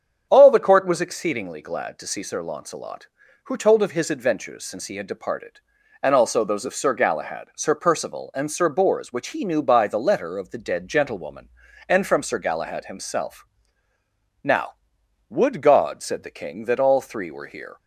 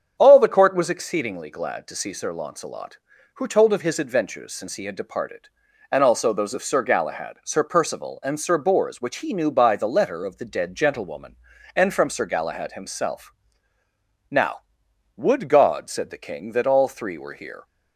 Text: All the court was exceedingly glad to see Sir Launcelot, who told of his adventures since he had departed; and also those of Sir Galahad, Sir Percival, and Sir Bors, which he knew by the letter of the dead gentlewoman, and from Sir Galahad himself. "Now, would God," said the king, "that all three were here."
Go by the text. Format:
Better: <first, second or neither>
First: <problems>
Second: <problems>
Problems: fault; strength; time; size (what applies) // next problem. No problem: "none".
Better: neither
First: starts louder than the rest; strong; until 1.3 s; 8 dB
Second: starts louder than the rest; strong; until 1.2 s; 8 dB